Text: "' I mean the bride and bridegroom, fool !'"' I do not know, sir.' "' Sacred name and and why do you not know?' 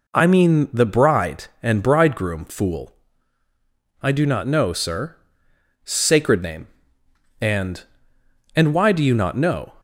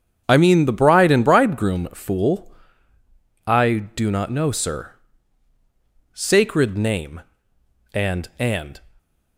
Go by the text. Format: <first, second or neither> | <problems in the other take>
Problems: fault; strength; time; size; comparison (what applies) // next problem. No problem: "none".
first | starts louder than the rest; strong; until 1.2 s; 8.5 dB // stops before "why do you not know"; at 8.9 s